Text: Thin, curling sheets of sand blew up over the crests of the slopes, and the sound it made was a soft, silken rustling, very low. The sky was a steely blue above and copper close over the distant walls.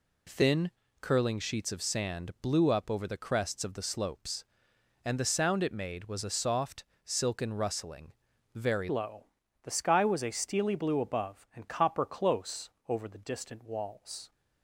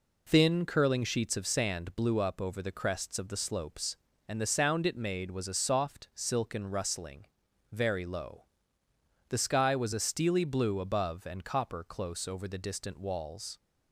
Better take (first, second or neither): second